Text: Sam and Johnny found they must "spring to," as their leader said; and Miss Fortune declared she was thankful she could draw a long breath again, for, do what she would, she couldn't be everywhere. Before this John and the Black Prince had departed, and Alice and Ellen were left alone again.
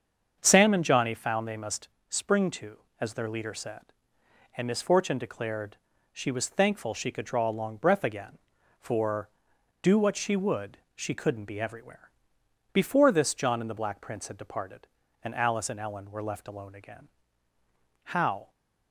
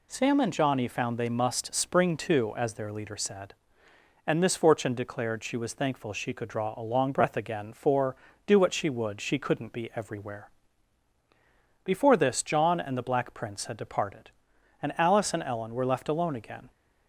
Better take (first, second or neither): second